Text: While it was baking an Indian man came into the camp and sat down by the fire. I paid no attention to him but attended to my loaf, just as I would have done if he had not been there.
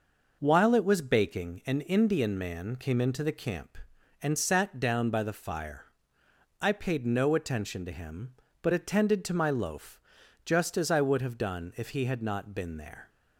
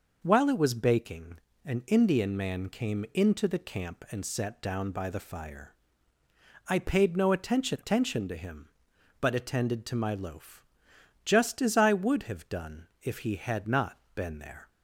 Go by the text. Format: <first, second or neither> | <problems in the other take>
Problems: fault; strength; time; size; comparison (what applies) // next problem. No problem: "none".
first | pauses between "baking" and "an"; slight; at 1.3 s; 0.26 s long // says "attention" twice; at 7.7 s // pauses between "done" and "if"; slight; at 12.8 s; 0.16 s long // pauses between "not" and "been"; slight; at 13.9 s; 0.16 s long